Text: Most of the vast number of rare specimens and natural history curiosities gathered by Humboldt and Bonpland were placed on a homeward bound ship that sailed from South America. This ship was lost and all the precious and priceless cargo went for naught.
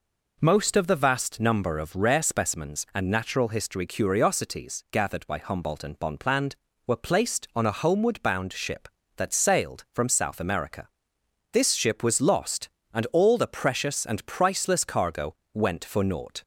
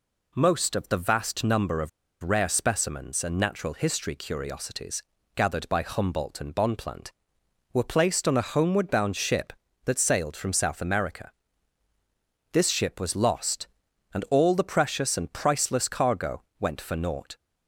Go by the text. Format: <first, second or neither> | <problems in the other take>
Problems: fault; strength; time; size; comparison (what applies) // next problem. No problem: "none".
first | pauses between "of" and "rare"; slight; at 1.8 s; 0.33 s long // pauses between "curiosities" and "gathered"; slight; at 5.0 s; 0.32 s long // pauses between "cargo" and "went"; slight; at 16.4 s; 0.18 s long; slight in the first